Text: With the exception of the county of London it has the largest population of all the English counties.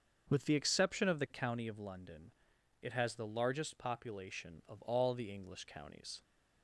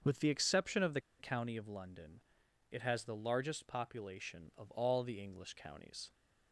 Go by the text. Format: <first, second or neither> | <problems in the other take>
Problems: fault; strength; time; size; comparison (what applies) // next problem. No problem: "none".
first | starts louder than the rest; until 1.2 s; 6.5 dB; also in the first // pauses between "the" and "county"; slight; at 1.0 s; 0.18 s long // pauses between "London" and "it"; noticeable; at 2.1 s; 0.50 s long; noticeable in the first